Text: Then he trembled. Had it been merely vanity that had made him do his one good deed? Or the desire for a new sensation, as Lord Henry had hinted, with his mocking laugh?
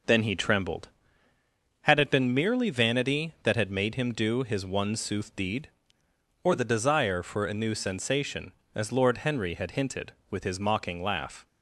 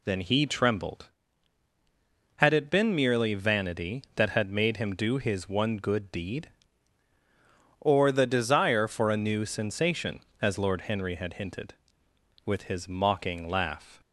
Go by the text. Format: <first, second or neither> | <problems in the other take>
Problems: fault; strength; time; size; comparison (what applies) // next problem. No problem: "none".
second | says "sooth" for "good"; at 4.9 s